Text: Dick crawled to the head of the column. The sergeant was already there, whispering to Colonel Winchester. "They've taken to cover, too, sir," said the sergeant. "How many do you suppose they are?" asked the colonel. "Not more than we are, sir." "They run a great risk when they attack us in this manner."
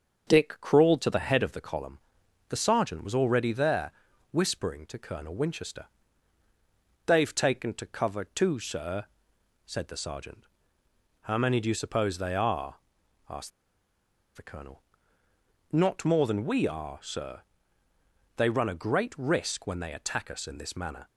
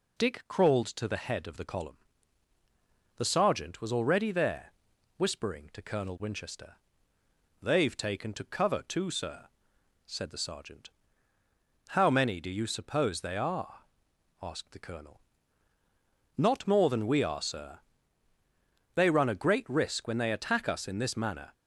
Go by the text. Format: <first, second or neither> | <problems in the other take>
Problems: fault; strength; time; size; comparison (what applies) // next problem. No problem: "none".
second | starts louder than the rest; until 1.3 s; 6.5 dB // pauses between "asked" and "the"; noticeable; at 13.5 s; 0.86 s long